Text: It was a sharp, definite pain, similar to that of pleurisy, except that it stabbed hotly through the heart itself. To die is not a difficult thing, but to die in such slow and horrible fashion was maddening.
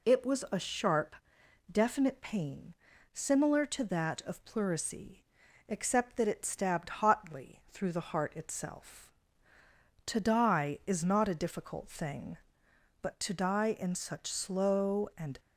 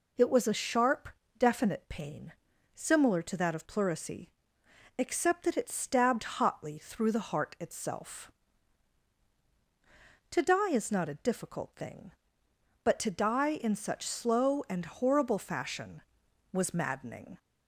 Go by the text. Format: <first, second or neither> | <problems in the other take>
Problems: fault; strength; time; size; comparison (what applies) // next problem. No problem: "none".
second | stops before "horrible fashion was maddening"; at 15.3 s